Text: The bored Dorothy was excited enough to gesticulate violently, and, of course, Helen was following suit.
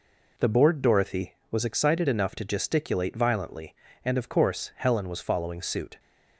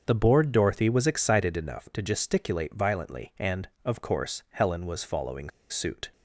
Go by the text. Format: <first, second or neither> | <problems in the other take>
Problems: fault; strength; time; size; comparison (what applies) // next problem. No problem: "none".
first | starts louder than the rest; until 1.0 s; 6.5 dB // pauses between "following" and "suit"; slight; at 5.4 s; 0.21 s long